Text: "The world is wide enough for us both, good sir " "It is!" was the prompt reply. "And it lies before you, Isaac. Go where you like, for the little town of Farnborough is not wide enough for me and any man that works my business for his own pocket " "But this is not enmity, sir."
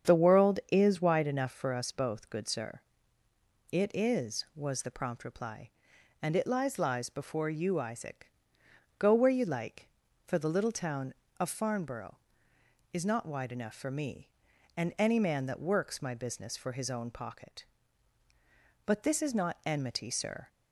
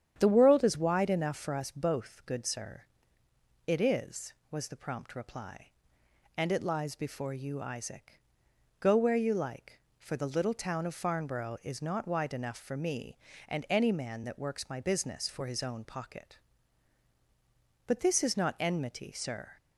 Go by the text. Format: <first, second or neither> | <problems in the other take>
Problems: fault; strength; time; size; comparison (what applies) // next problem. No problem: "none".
second | starts louder than the rest; strong; until 1.1 s; 8 dB; strong in the second // says "lies" twice; at 6.7 s